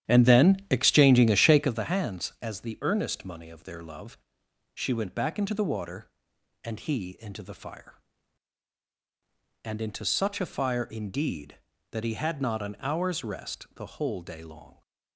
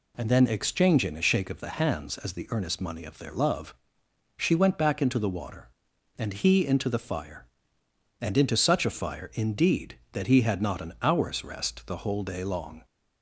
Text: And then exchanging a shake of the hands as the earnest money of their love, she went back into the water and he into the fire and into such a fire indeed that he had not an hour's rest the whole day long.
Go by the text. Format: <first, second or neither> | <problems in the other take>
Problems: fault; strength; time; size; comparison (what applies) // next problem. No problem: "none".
second | starts louder than the rest; strong; until 1.8 s; 10.5 dB